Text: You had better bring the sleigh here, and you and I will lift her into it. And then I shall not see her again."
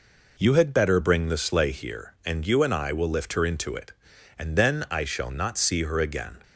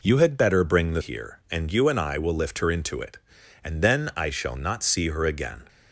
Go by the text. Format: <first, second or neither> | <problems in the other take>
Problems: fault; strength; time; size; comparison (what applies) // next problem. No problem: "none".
first | skips "sleigh"; at 1.0 s